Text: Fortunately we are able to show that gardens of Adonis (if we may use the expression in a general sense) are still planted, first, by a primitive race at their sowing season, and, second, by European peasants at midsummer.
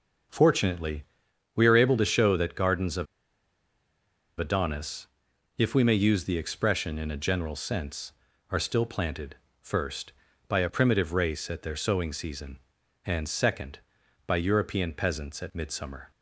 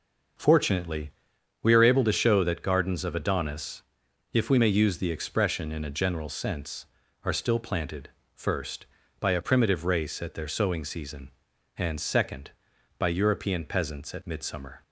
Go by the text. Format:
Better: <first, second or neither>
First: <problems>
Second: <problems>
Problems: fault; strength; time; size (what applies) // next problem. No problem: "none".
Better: second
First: starts louder than the rest; until 1.8 s; 6.5 dB // pauses between "Fortunately" and "we"; noticeable; at 1.0 s; 0.54 s long // pauses between "of" and "Adonis"; strong; at 3.0 s; 1.3 s long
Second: starts louder than the rest; until 1.9 s; 6.5 dB // pauses between "Fortunately" and "we"; noticeable; at 1.0 s; 0.54 s long